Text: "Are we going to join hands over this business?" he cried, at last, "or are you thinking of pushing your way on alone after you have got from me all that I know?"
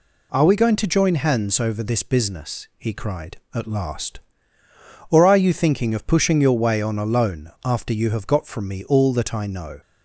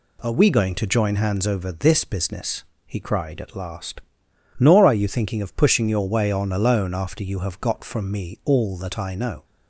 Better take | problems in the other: first | says "nor" for "or"; at 4.5 s

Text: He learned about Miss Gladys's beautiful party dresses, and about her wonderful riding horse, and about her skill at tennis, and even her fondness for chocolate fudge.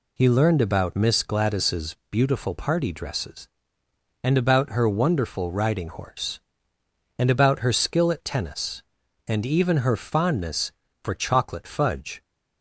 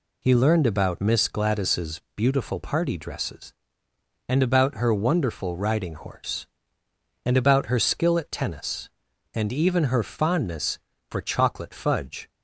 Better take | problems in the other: neither | none

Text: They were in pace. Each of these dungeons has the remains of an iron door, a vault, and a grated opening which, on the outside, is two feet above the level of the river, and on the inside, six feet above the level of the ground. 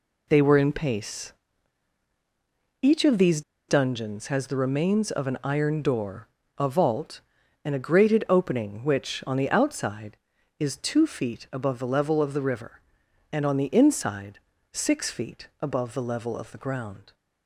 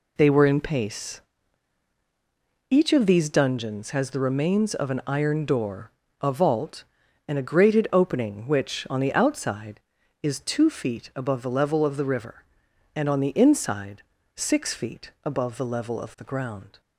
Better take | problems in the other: second | pauses between "these" and "dungeons"; slight; at 3.4 s; 0.27 s long

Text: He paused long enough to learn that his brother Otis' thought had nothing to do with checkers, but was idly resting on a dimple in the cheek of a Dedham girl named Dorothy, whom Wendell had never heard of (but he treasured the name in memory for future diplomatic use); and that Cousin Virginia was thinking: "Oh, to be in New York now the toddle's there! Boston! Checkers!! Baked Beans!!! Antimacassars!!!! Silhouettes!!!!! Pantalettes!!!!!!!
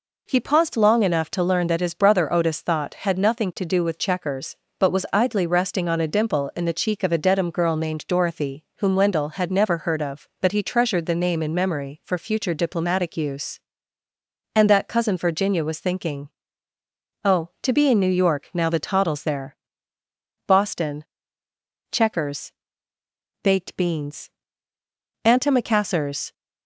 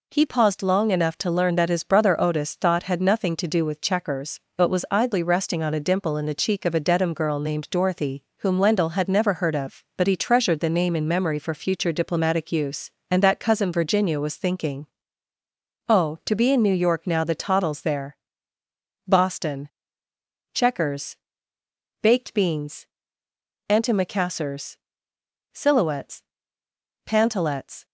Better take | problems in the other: second | stops before "Silhouettes Pantalettes"; at 26.3 s

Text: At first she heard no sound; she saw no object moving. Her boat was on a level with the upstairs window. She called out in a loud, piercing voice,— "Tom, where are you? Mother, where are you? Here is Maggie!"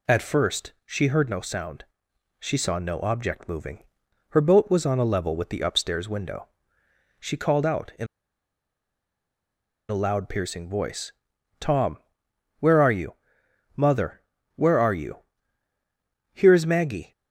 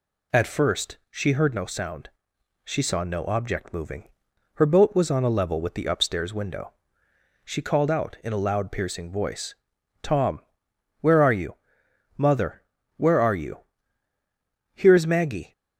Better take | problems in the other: second | pauses between "in" and "a"; strong; at 8.0 s; 1.8 s long

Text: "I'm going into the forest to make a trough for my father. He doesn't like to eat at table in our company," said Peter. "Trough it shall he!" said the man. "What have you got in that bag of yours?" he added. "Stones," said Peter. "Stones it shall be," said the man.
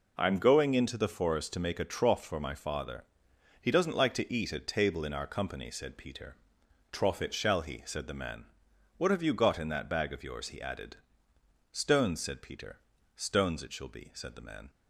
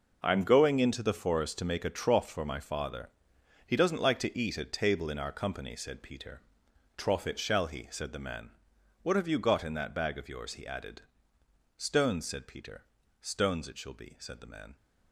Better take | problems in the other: first | gets quieter; strong; throughout; 12 dB

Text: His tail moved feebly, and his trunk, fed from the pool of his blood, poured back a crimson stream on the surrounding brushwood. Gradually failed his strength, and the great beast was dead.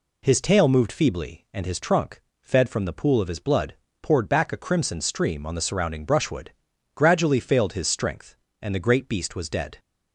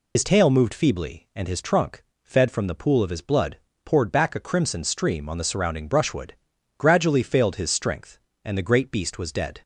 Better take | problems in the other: first | loses the start of "His"; at 0.1 s; 85 ms

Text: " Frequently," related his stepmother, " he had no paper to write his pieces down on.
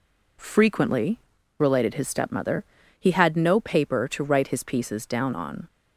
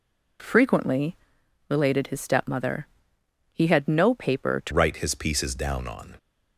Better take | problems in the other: first | changes voice at "write"; from 4.7 s on; 1.4 s long

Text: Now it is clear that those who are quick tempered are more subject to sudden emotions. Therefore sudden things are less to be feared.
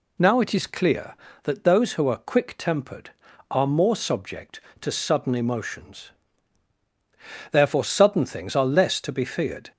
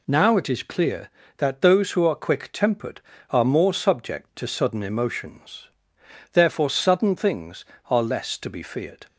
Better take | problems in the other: neither | none

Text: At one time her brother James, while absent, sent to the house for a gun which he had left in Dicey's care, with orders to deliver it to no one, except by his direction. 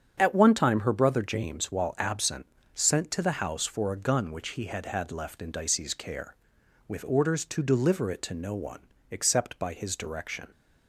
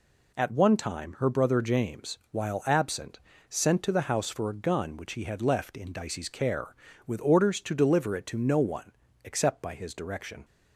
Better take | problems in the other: second | starts louder than the rest; strong; until 1.2 s; 7.5 dB // says "had" twice; at 4.8 s

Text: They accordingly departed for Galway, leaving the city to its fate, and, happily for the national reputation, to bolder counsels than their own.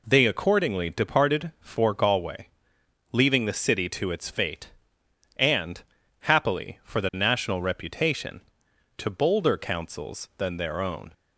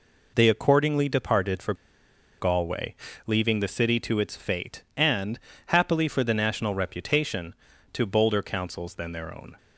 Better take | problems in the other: first | pauses between "for" and "Galway"; noticeable; at 1.7 s; 0.66 s long

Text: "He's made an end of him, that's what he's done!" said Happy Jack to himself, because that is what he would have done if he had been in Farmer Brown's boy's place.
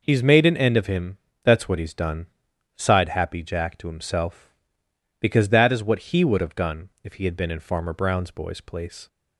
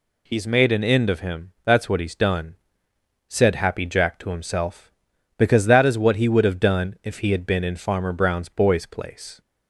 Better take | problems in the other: second | says "sighed" for "said"; at 2.7 s // pauses between "done" and "if"; slight; at 6.8 s; 0.16 s long

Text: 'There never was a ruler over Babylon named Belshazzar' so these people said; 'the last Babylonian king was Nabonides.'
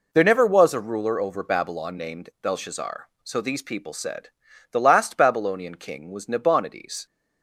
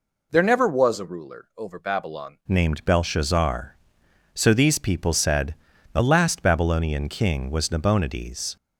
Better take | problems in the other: first | changes voice at "named"; from 2.4 s on; 6.1 s long

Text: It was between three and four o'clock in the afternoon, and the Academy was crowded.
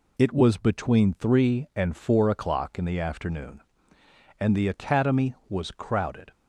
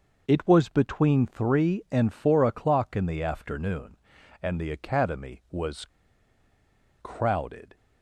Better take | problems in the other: first | pauses between "was" and "crowded"; at 5.8 s; 1.1 s long

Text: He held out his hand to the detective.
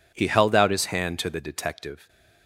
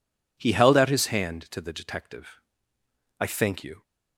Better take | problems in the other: first | goes on to say "I thank you"; noticeable; from 3.1 s on; 0.64 s long

